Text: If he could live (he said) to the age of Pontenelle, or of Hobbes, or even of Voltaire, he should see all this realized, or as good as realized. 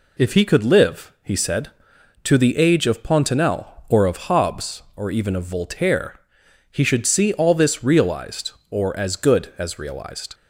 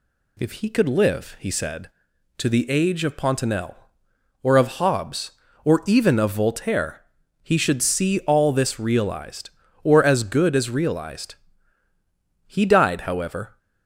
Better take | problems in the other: first | goes on to say "He died however"; noticeable; from 12.4 s on; 1.1 s long

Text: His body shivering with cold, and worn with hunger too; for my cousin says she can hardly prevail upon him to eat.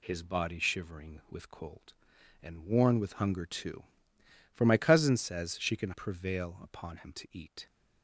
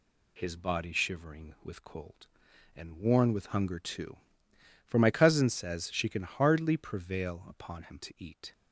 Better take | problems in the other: second | skips "hardly"; at 5.9 s

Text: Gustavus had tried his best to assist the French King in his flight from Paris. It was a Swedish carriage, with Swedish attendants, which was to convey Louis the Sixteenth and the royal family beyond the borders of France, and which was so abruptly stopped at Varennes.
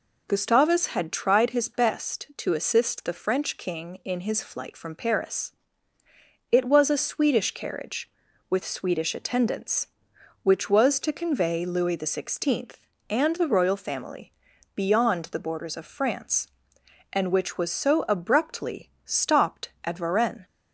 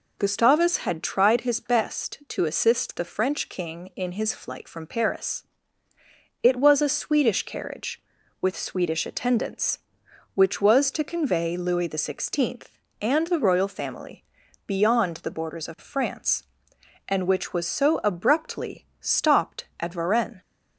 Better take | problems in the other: neither | pauses between "family" and "beyond"; the same in both // pauses between "abruptly" and "stopped"; slight; the same in both

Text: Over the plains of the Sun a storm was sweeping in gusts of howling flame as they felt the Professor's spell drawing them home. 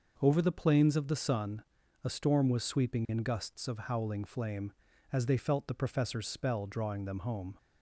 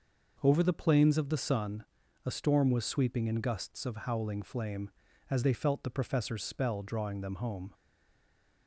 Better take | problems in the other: first | pauses between "Sun" and "a"; at 1.8 s; 0.40 s long; also in the first // stays silent after the last word; slight; from 7.7 s on; 0.9 s long

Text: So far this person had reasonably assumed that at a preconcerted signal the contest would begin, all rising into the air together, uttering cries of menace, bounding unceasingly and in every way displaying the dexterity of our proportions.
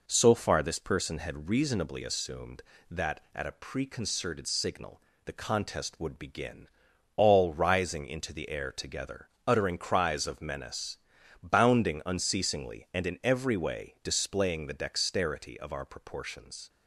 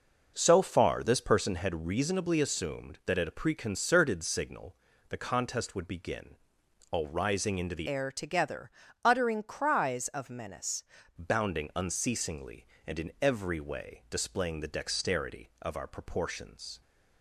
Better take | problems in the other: first | pauses between "signal" and "the"; slight; at 4.7 s; 0.34 s long; slight in the first // changes voice from "air" to "menace"; from 7.8 to 10.8 s; 3.0 s long

